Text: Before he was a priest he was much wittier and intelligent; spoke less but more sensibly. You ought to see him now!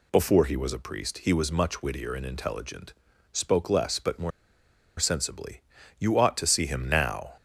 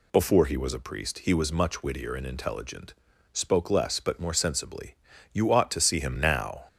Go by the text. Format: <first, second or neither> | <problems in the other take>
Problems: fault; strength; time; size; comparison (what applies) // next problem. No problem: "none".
second | pauses between "more" and "sensibly"; noticeable; at 4.3 s; 0.69 s long